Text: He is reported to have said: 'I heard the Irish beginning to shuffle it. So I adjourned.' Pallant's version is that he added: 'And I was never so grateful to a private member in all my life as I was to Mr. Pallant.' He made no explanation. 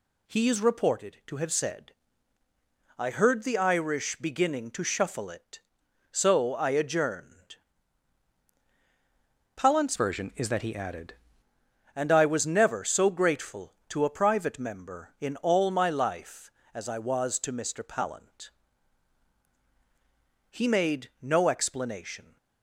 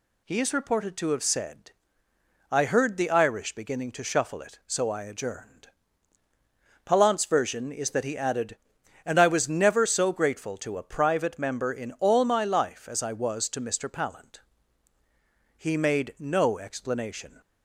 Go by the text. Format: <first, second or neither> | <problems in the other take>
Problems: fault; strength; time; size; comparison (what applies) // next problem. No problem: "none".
second | changes voice from "version" to "added"; from 9.9 to 11.1 s; 1.2 s long